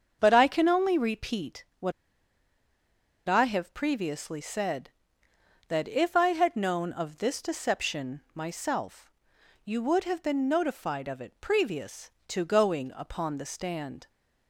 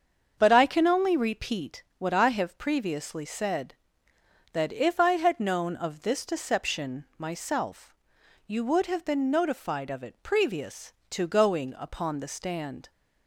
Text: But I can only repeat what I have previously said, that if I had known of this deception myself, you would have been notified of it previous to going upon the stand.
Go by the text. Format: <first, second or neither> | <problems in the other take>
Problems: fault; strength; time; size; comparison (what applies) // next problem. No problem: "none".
second | starts louder than the rest; until 1.2 s; 7 dB; strong in the second // pauses between "repeat" and "what"; slight; at 1.6 s; 0.16 s long; slight in the second // pauses between "what" and "I"; strong; at 1.9 s; 1.3 s long